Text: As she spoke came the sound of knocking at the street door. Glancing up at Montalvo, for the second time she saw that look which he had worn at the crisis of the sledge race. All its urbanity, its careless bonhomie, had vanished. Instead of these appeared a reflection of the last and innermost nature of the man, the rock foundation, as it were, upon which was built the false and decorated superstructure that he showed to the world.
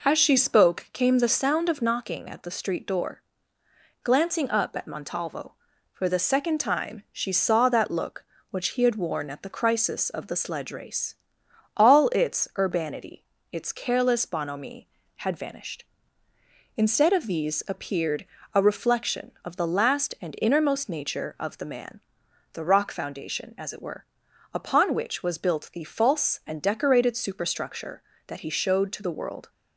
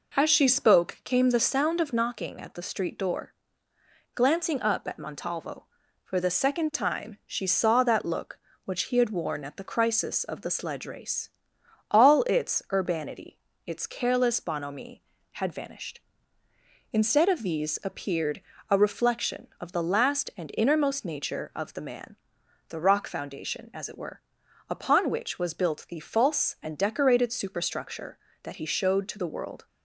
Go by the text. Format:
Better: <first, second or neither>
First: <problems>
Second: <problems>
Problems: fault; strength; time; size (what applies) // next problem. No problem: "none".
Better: neither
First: pauses between "appeared" and "a"; slight; at 18.2 s; 0.30 s long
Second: pauses between "appeared" and "a"; slight; at 18.3 s; 0.30 s long